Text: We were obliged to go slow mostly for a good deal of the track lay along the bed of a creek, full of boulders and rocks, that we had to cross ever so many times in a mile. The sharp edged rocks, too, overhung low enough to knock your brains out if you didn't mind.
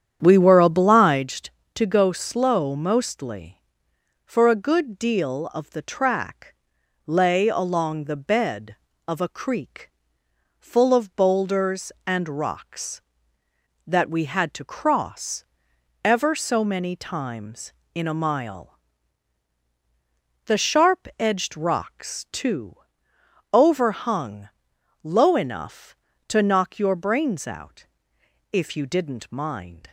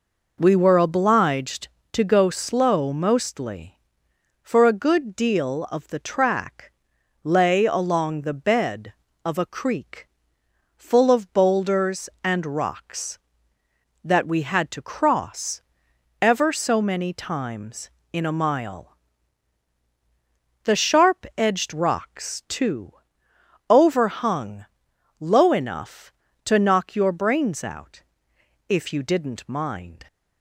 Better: second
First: starts louder than the rest; strong; until 1.3 s; 9 dB // pauses between "track" and "lay"; noticeable; at 6.5 s; 0.54 s long // pauses between "cross" and "ever"; noticeable; at 15.4 s; 0.62 s long // pauses between "overhung" and "low"; noticeable; at 24.5 s; 0.52 s long // pauses between "out" and "if"; noticeable; at 27.8 s; 0.66 s long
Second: pauses between "track" and "lay"; noticeable; at 6.7 s; 0.54 s long // pauses between "cross" and "ever"; noticeable; at 15.6 s; 0.62 s long // pauses between "overhung" and "low"; noticeable; at 24.6 s; 0.52 s long // pauses between "out" and "if"; noticeable; at 28.0 s; 0.66 s long

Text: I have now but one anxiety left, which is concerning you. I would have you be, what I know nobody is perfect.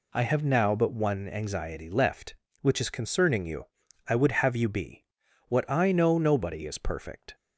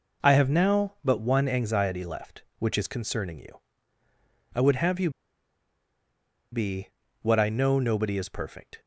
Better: first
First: none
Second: pauses between "you" and "be"; strong; at 5.1 s; 1.4 s long

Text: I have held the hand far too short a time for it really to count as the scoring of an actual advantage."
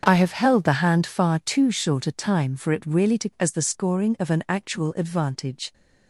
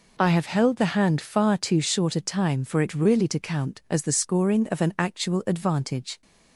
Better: second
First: starts louder than the rest; strong; until 1.0 s; 7.5 dB // skips "count"; at 3.3 s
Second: none

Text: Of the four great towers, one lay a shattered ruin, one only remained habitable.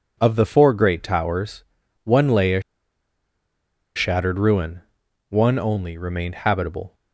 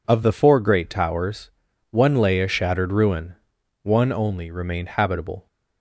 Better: second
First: pauses between "a" and "shattered"; strong; at 2.6 s; 1.3 s long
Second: none

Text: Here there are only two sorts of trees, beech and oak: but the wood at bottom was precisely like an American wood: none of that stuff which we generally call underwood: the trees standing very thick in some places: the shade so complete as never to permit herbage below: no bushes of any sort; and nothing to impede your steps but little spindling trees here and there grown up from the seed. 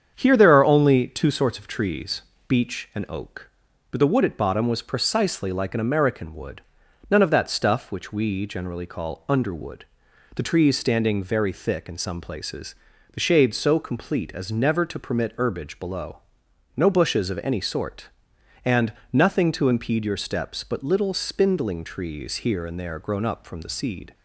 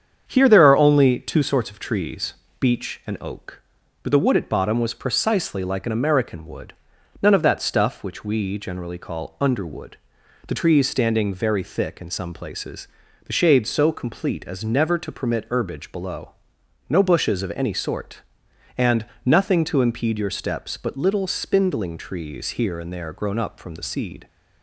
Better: neither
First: starts louder than the rest; strong; until 1.1 s; 7.5 dB // pauses between "and" and "nothing"; slight; at 18.9 s; 0.22 s long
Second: starts louder than the rest; strong; until 1.2 s; 7.5 dB // pauses between "and" and "nothing"; slight; at 19.0 s; 0.22 s long

